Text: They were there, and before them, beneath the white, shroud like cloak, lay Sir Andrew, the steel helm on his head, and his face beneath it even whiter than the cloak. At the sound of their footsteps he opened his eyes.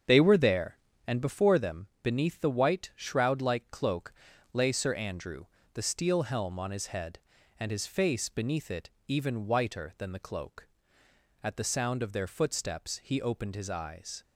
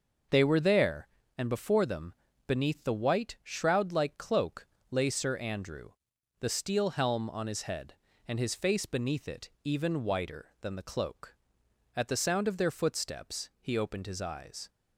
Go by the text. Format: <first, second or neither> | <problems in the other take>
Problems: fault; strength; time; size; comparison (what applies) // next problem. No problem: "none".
second | starts louder than the rest; strong; until 1.4 s; 7.5 dB // pauses between "it" and "even"; slight; at 8.8 s; 0.18 s long